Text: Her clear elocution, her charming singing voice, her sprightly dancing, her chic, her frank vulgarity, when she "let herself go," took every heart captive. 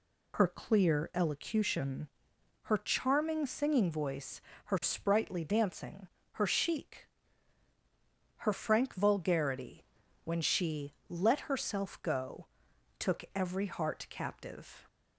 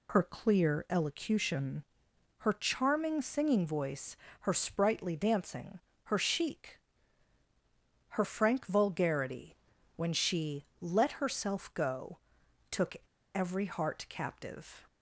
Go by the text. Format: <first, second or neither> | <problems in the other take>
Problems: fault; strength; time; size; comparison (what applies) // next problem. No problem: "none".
first | pauses between "she" and "let"; slight; at 10.6 s; 0.16 s long; slight in the first // pauses between "took" and "every"; at 12.9 s; 0.37 s long